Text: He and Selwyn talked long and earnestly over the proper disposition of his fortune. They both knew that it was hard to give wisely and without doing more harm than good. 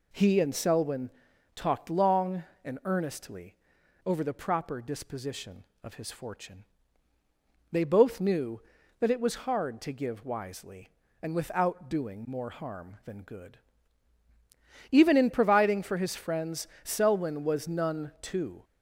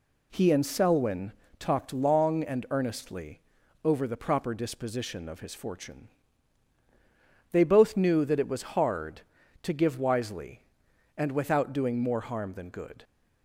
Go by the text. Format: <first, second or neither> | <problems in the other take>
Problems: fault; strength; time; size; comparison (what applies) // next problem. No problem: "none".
second | pauses between "Selwyn" and "talked"; noticeable; at 1.1 s; 0.46 s long; slight in the second // pauses between "earnestly" and "over"; noticeable; at 3.5 s; 0.48 s long; also in the second // goes on to say "Even in providing for his friends Selwyn was none too"; strong; from 14.9 s on; 3.7 s long